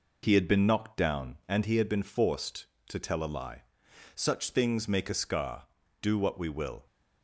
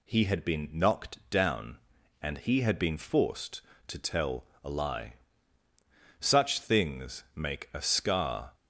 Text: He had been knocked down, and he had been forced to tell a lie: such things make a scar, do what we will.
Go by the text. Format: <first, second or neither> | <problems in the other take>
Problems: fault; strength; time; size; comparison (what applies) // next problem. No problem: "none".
first | pauses between "tell" and "a"; slight; at 4.4 s; 0.18 s long // stops before "do what we will"; at 8.5 s